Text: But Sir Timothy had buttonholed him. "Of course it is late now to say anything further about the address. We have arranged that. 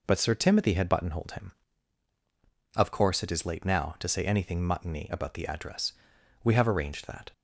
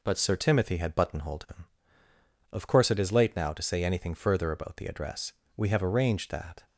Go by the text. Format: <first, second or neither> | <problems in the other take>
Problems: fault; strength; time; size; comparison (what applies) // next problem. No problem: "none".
second | says "muttony" for "further"; at 4.6 s